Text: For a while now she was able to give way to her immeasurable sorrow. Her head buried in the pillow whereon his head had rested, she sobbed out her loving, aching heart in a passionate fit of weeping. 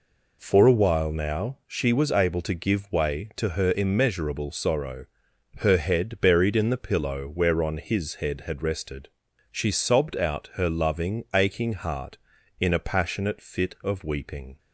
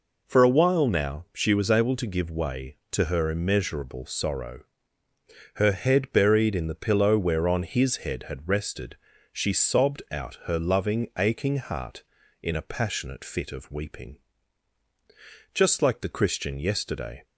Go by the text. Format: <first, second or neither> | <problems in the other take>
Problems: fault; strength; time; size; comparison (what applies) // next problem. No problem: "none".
first | goes on to say "Just like the Christian yesterday"; strong; from 15.5 s on; 1.7 s long